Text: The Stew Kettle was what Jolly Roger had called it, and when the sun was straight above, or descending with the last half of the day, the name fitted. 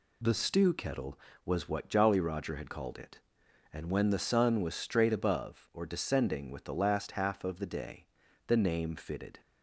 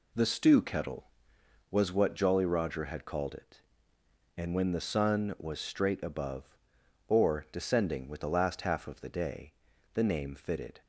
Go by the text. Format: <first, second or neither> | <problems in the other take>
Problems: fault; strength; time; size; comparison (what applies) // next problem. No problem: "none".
neither | none